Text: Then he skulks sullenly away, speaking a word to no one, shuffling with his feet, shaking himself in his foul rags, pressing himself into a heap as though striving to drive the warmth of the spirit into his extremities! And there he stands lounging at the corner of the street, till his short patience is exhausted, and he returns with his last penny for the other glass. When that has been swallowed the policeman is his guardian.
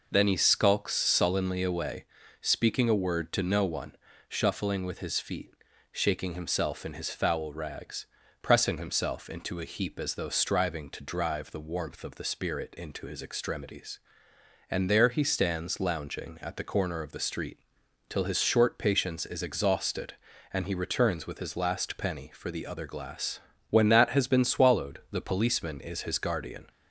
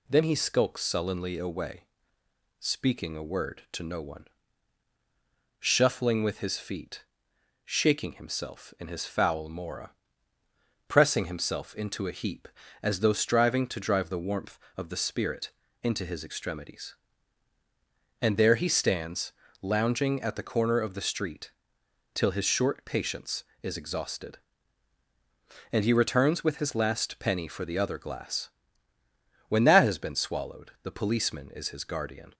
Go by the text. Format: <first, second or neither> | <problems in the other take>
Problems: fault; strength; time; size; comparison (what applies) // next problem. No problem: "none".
first | says "mora" for "rags"; at 9.4 s // pauses between "spirit" and "into"; slight; at 15.5 s; 0.30 s long // pauses between "stands" and "lounging"; slight; at 19.3 s; 0.30 s long